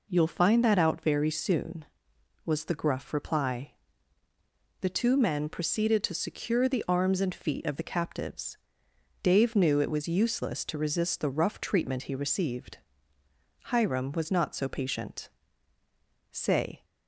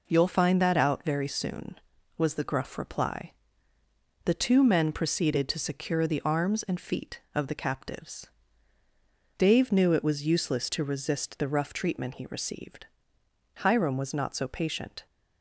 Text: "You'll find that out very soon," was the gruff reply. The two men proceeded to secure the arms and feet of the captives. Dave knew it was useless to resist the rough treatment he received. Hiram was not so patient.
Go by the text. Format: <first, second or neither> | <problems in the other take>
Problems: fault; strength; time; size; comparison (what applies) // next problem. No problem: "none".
second | goes on to say "Say"; from 16.3 s on; 0.54 s long